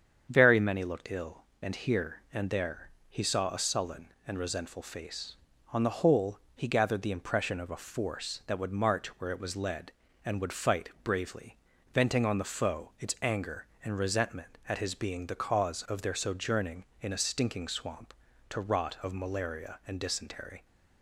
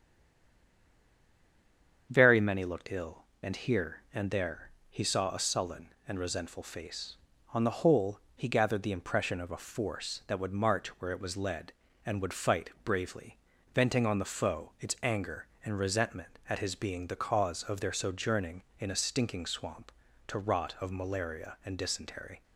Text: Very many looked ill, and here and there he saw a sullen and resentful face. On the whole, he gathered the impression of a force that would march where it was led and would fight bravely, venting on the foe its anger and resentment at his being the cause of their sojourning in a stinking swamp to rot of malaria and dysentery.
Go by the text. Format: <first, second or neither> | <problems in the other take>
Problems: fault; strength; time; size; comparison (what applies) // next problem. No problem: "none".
first | stays silent before the first word; noticeable; until 2.0 s; 2.0 s long // starts louder than the rest; strong; until 3.1 s; 7.5 dB; strong in the first // pauses between "there" and "he"; slight; at 4.6 s; 0.20 s long; slight in the first